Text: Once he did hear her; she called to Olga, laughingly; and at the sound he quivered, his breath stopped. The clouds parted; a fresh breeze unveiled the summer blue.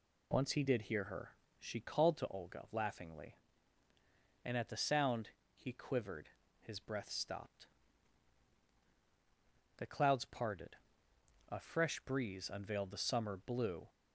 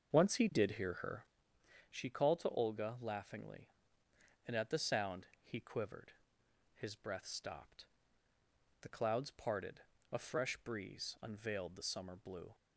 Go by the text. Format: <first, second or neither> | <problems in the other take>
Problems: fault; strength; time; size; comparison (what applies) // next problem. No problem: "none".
first | starts louder than the rest; until 1.6 s; 6.5 dB // pauses between "sound" and "he"; slight; at 5.2 s; 0.16 s long; slight in the first